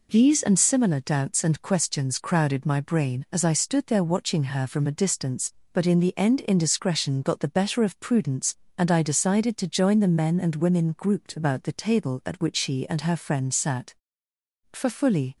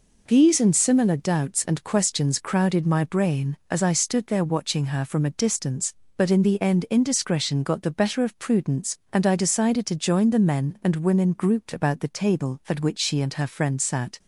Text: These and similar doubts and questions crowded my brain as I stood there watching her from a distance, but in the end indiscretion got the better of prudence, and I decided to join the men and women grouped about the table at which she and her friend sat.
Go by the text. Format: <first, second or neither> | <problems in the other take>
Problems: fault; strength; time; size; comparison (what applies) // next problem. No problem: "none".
second | goes on to say "For fully"; noticeable; from 14.7 s on; 0.64 s long